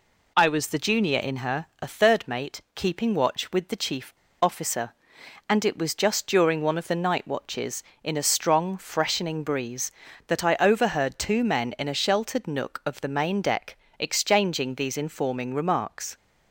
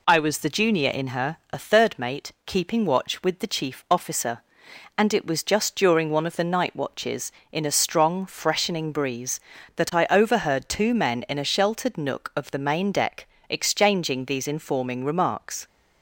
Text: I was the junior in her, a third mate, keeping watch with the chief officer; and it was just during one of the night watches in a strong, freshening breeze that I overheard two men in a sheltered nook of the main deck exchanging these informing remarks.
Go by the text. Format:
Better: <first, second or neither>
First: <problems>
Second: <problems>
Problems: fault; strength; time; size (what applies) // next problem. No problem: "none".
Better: second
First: pauses between "chief" and "officer"; slight; at 4.1 s; 0.26 s long // pauses between "deck" and "exchanging"; slight; at 13.7 s; 0.24 s long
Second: pauses between "deck" and "exchanging"; slight; at 13.2 s; 0.24 s long